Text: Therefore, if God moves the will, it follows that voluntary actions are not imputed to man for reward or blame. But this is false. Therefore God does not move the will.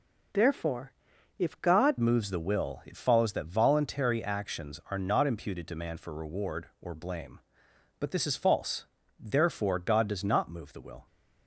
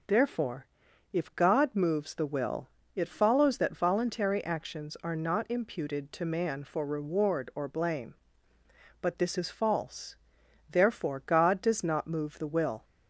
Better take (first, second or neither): second